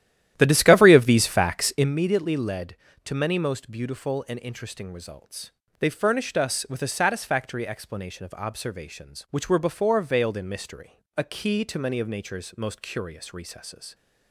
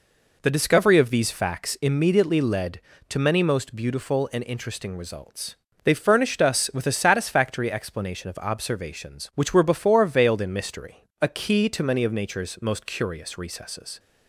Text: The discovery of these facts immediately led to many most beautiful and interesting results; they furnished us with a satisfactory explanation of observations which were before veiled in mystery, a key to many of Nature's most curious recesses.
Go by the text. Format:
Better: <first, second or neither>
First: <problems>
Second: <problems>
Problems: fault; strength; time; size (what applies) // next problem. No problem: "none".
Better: second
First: starts louder than the rest; strong; until 1.9 s; 12 dB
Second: none